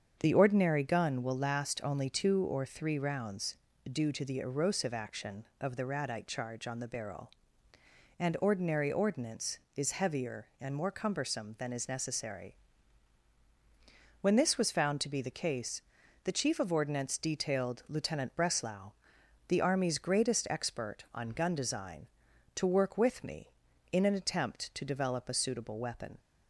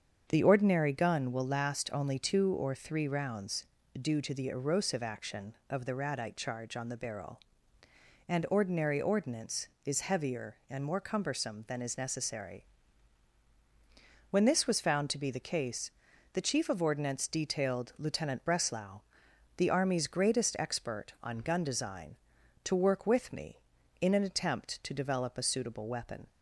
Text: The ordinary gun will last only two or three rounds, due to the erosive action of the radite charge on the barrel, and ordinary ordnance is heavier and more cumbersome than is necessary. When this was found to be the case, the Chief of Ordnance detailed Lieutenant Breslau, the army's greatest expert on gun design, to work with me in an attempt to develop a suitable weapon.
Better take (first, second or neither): neither